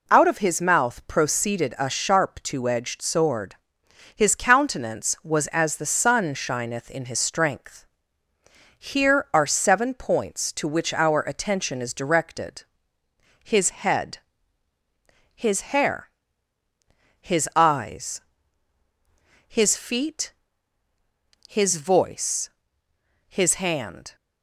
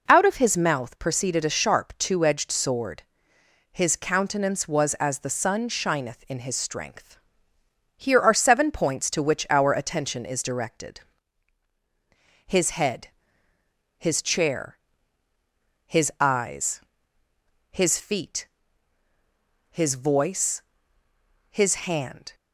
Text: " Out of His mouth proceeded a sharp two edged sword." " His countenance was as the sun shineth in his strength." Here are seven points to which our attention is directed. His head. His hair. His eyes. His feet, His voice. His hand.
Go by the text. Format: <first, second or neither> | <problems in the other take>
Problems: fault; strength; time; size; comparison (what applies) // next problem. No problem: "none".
first | says "chair" for "hair"; at 14.2 s // pauses between "His" and "hand"; slight; at 21.7 s; 0.16 s long